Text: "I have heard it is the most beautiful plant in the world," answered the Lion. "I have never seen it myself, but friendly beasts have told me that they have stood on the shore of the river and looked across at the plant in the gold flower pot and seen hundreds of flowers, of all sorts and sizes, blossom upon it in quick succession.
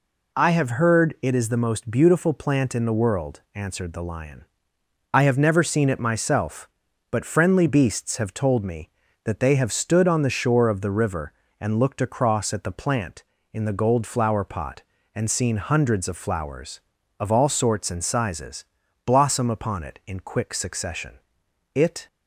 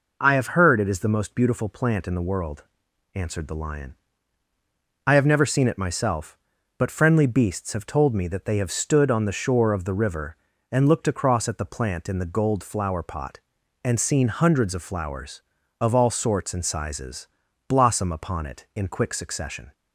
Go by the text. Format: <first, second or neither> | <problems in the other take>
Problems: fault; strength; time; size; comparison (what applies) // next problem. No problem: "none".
second | goes on to say "It"; slight; from 21.7 s on; 0.32 s long